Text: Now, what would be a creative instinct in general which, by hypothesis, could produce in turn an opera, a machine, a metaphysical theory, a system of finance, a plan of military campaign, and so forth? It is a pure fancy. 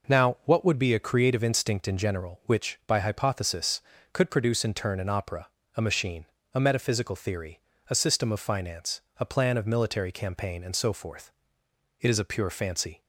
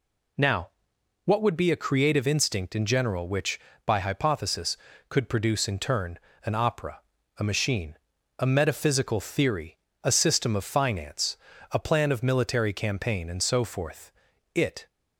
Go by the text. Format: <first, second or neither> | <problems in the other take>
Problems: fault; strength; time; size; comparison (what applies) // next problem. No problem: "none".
first | pauses between "turn" and "an"; slight; at 6.1 s; 0.26 s long // stops before "is a pure fancy"; at 14.9 s